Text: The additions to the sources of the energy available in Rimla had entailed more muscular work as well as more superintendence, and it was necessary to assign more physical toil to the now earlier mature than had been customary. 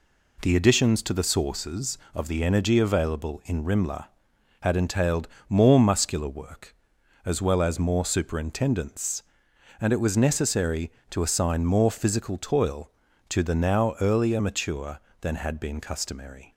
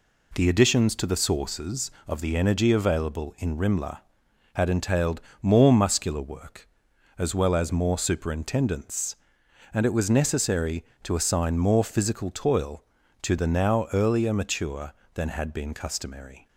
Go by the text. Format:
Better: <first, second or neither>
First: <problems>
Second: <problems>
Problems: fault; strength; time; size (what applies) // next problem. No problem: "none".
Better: neither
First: pauses between "entailed" and "more"; slight; at 5.2 s; 0.22 s long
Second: pauses between "entailed" and "more"; slight; at 5.2 s; 0.22 s long